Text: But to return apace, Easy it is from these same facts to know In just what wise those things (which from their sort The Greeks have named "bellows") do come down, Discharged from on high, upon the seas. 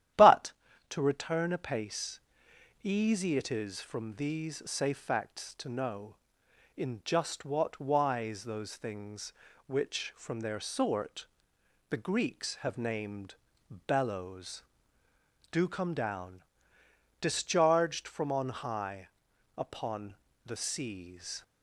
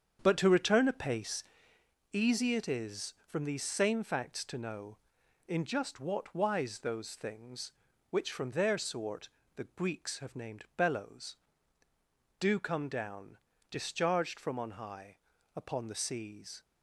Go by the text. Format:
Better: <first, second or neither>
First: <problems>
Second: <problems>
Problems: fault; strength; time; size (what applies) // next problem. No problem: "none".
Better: second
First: starts louder than the rest; strong; until 1.5 s; 11.5 dB // says "safe" for "same"; at 4.6 s // pauses between "sort" and "The"; noticeable; at 11.2 s; 0.64 s long // pauses between "named" and "bellows"; noticeable; at 13.3 s; 0.52 s long // pauses between "upon" and "the"; slight; at 20.1 s; 0.32 s long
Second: starts louder than the rest; strong; until 1.2 s; 7.5 dB // pauses between "sort" and "The"; slight; at 9.2 s; 0.26 s long